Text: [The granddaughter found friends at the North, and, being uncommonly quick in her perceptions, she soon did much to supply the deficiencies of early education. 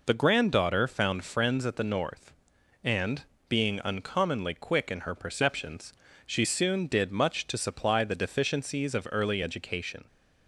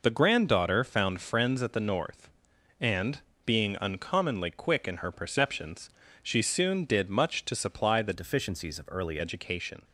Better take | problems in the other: first | changes voice from "deficiencies" to "early"; from 8.1 to 9.1 s; 1.0 s long

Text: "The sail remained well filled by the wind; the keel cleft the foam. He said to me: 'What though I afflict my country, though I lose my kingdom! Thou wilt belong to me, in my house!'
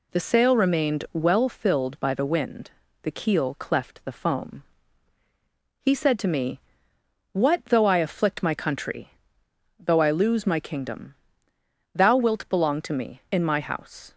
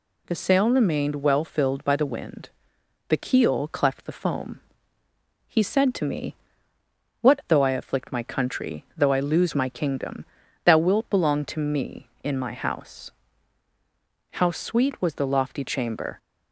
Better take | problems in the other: first | goes on to say "How sweet was the lofty chamber"; strong; from 14.3 s on; 1.8 s long

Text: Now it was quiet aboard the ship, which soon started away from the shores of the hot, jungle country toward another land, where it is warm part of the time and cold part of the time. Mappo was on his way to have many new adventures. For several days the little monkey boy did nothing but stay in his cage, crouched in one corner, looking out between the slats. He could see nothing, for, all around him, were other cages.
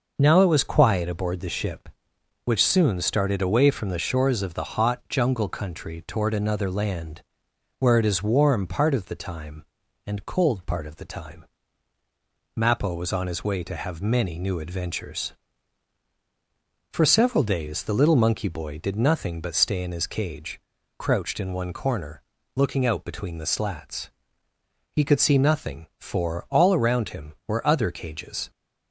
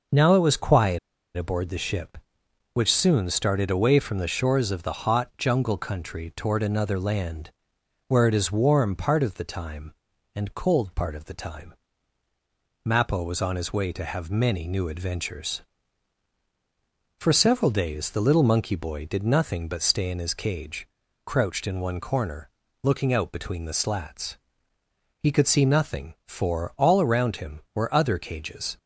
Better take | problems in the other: first | pauses between "quiet" and "aboard"; at 0.9 s; 0.38 s long

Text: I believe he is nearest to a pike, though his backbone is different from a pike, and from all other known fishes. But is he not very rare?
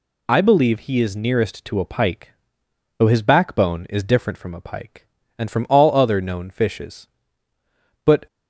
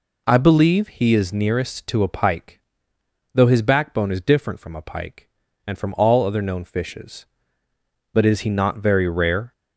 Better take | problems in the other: second | stops before "is he not very rare"; at 8.2 s

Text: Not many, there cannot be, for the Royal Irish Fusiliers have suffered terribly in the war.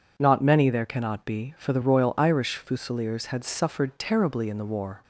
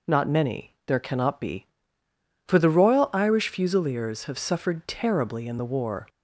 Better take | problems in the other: second | says "had" for "have"; at 3.2 s

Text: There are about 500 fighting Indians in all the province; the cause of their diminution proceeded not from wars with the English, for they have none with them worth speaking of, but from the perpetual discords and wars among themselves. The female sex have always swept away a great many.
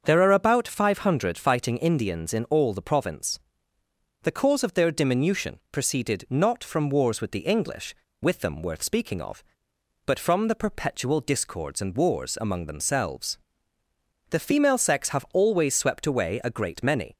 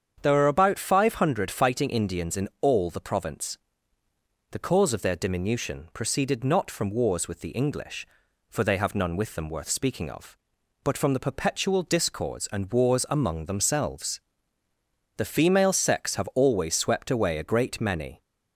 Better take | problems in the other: second | starts louder than the rest; until 1.0 s; 7 dB; strong in the second // skips "for they have none"; at 8.0 s

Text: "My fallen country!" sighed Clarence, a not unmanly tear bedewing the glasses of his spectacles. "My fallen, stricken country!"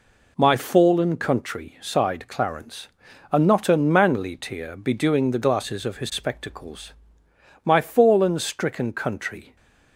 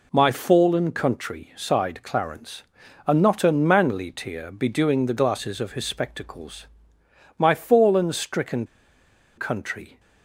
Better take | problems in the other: first | pauses between "stricken" and "country"; noticeable; at 8.6 s; 0.72 s long

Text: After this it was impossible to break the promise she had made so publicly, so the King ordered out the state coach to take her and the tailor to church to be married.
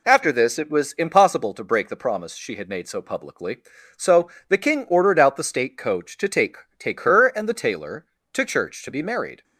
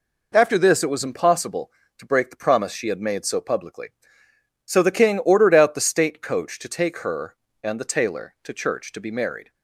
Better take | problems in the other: second | pauses between "so" and "the"; slight; at 4.2 s; 0.20 s long // says "take" twice; at 6.7 s

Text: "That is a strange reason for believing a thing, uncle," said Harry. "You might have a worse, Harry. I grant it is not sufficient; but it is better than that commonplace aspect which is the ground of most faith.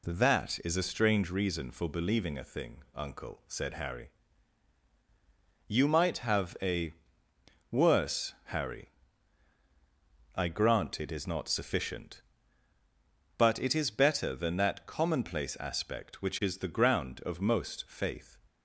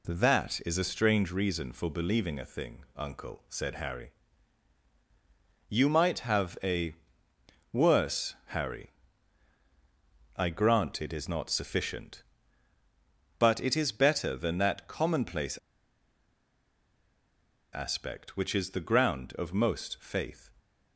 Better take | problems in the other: first | pauses between "a" and "worse"; noticeable; at 6.9 s; 0.78 s long; noticeable in the first // pauses between "commonplace" and "aspect"; strong; at 15.5 s; 2.1 s long

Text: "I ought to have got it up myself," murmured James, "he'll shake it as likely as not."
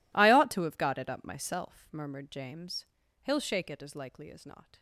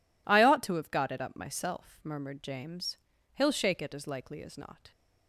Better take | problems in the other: second | gets quieter; strong; throughout; 19.5 dB

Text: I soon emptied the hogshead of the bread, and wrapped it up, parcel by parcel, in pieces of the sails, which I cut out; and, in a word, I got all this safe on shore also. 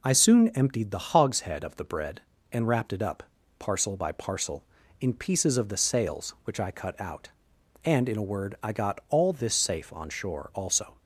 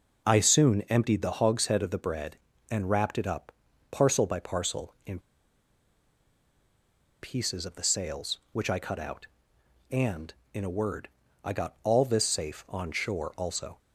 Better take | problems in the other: first | pauses between "in" and "pieces"; strong; at 5.1 s; 2.0 s long

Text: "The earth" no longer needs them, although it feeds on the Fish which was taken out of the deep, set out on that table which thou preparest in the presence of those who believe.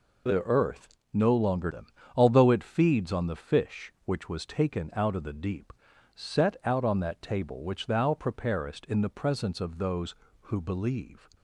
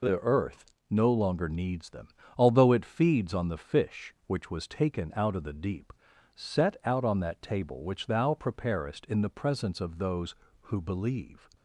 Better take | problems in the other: second | pauses between "earth" and "no"; slight; at 0.9 s; 0.16 s long; slight in the second // skips "needs"; at 1.7 s

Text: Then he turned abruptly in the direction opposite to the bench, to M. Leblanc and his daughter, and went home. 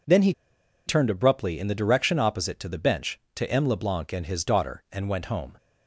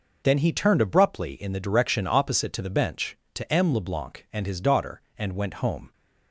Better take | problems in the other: second | pauses between "he" and "turned"; noticeable; at 0.3 s; 0.54 s long

